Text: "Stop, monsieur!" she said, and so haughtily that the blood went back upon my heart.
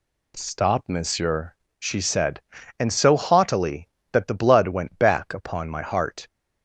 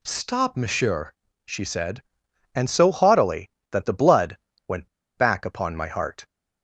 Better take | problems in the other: first | pauses between "blood" and "went"; slight; at 4.3 s; 0.30 s long // pauses between "went" and "back"; slight; at 4.8 s; 0.29 s long

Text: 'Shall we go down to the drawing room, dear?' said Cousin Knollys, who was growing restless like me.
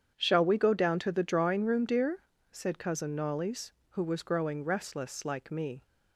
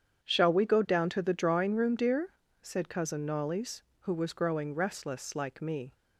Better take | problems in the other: neither | starts louder than the rest; strong; the same in both

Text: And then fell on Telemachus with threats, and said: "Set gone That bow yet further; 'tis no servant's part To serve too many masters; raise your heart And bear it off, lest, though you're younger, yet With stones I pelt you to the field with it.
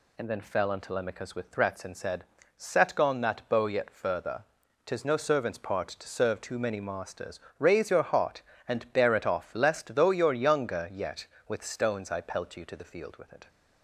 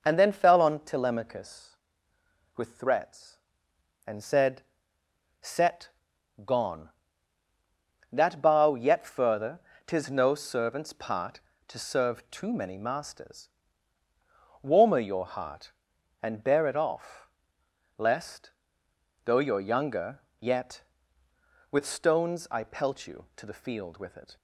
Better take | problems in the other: first | pauses between "Set" and "gone"; noticeable; at 5.8 s; 0.54 s long // says "warmer" for "raise"; at 14.5 s

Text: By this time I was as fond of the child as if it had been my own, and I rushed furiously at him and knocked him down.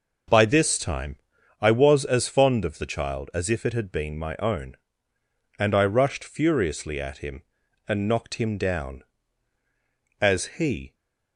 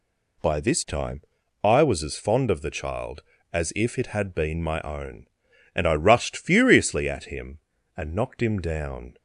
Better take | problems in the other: second | pauses between "time" and "I"; at 1.1 s; 0.42 s long; also in the second // goes on to say "As he"; noticeable; from 10.1 s on; 0.74 s long

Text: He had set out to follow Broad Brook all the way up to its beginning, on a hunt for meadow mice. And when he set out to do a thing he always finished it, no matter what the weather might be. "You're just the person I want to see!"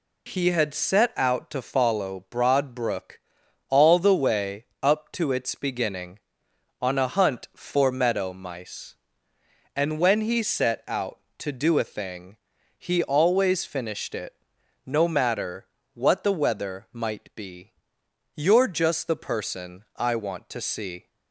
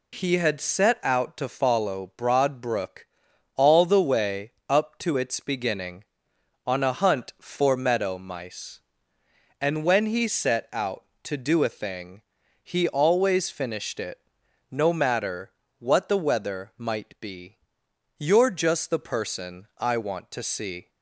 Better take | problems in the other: neither | pauses between "Brook" and "all"; noticeable; the same in both // pauses between "way" and "up"; slight; the same in both // pauses between "thing" and "he"; the same in both // pauses between "matter" and "what"; slight; the same in both

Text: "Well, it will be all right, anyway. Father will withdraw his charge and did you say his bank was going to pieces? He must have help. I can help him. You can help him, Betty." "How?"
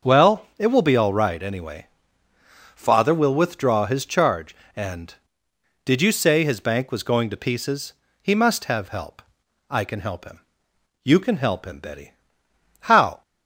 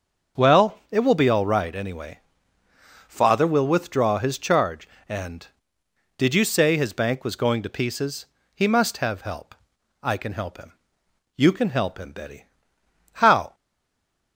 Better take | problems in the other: first | starts louder than the rest; until 1.4 s; 6 dB; also in the first // stays silent after the last word; slight; from 13.5 s on; 0.8 s long

